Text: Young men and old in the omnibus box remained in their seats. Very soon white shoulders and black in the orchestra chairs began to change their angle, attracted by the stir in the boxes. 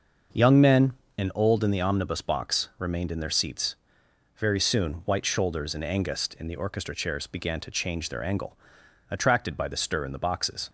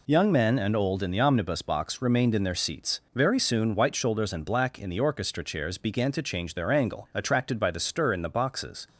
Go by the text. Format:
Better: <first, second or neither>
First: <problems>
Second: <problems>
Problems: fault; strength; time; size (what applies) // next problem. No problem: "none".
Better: second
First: starts louder than the rest; until 1.6 s; 6 dB // says "angust" for "black"; at 5.8 s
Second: none